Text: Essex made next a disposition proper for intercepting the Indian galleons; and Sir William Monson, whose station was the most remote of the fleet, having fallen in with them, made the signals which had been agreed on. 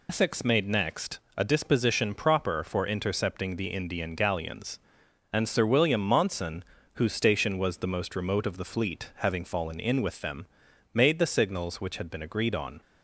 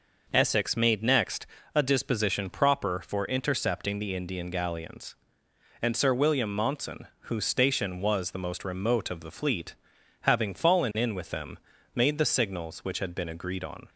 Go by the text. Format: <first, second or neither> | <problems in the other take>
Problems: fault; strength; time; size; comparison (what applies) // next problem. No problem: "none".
second | loses the start of "Essex"; at 0.0 s; 85 ms // pauses between "next" and "a"; slight; at 1.1 s; 0.18 s long; slight in the second